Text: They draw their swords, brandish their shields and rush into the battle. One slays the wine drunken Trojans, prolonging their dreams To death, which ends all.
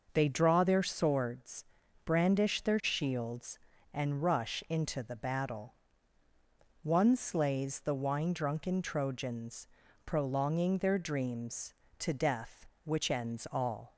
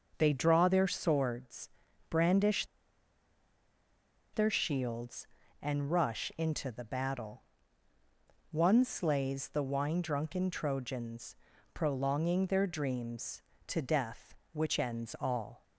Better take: first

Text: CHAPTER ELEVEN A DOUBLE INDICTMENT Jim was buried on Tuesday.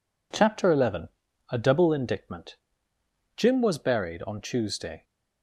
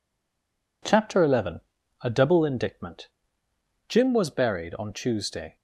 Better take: first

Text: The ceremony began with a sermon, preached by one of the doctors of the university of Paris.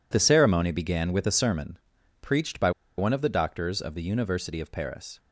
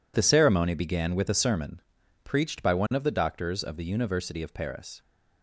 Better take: second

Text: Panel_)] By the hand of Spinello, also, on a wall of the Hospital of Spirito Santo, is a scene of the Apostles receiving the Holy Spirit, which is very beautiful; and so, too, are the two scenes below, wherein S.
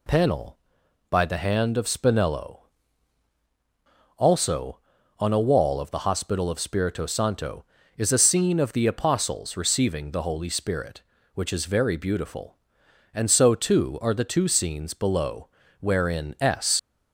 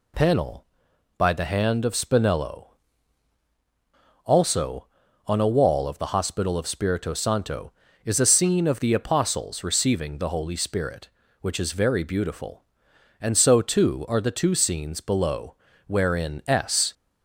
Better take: second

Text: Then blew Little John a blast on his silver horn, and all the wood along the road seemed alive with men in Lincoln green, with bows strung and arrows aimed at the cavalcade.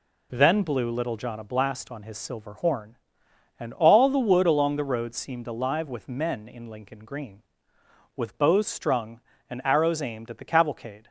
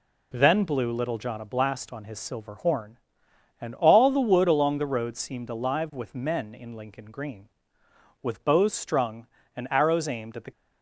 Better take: first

